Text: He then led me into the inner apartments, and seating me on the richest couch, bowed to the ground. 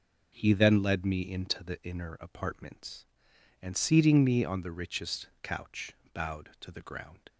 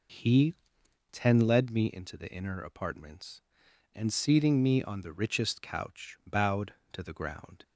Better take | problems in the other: first | says "ten" for "then"; at 1.1 s

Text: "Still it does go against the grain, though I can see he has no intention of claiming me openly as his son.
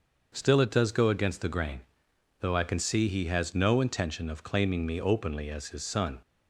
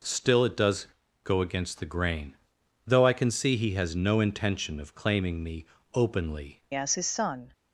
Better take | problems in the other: first | pauses between "does" and "go"; slight; at 0.8 s; 0.36 s long // pauses between "me" and "openly"; slight; at 5.6 s; 0.30 s long // changes voice at "as"; from 6.7 s on; 0.8 s long

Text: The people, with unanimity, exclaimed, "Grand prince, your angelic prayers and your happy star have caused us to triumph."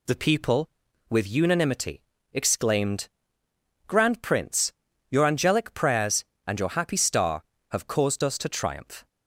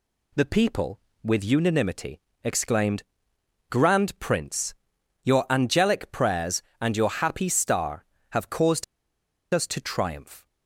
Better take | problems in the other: first | pauses between "caused" and "us"; noticeable; at 8.8 s; 0.69 s long

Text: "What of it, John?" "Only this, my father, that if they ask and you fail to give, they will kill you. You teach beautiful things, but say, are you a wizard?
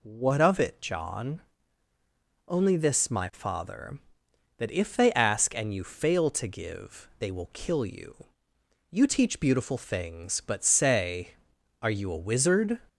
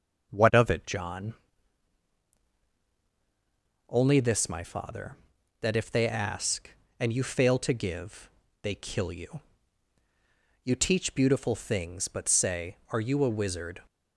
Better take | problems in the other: first | skips "will"; at 8.7 s

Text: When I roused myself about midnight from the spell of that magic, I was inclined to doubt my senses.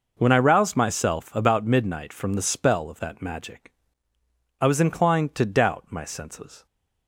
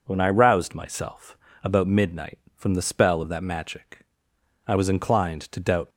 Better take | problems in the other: first | pauses between "myself" and "about"; slight; at 1.3 s; 0.28 s long // stops before "my senses"; at 5.9 s

